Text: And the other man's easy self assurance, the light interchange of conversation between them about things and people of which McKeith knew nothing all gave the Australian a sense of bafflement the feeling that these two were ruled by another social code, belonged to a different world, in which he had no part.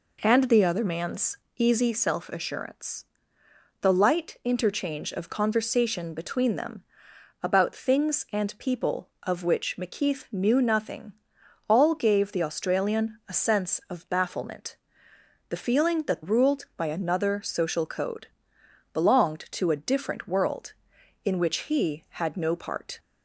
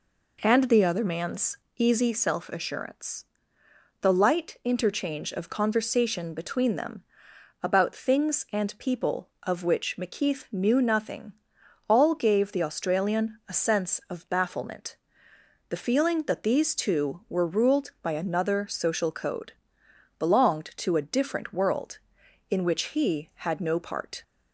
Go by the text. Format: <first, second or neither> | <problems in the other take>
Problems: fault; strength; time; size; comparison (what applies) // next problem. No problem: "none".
second | pauses between "man's" and "easy"; slight; at 1.3 s; 0.20 s long; slight in the second // pauses between "them" and "about"; noticeable; at 6.8 s; 0.58 s long; noticeable in the second // pauses between "nothing" and "all"; noticeable; at 11.1 s; 0.56 s long; noticeable in the second // pauses between "bafflement" and "the"; noticeable; at 14.7 s; 0.72 s long; noticeable in the second // skips "these two were"; at 16.2 s